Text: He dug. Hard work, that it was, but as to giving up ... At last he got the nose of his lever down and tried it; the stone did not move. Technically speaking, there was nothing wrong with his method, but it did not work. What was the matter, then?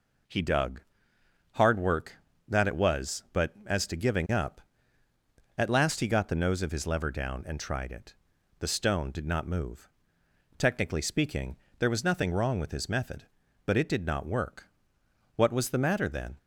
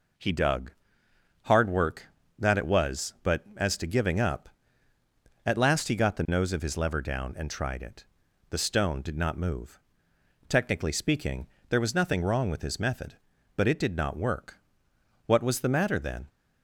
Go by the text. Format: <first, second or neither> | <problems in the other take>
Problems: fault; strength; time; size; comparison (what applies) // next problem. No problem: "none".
neither | none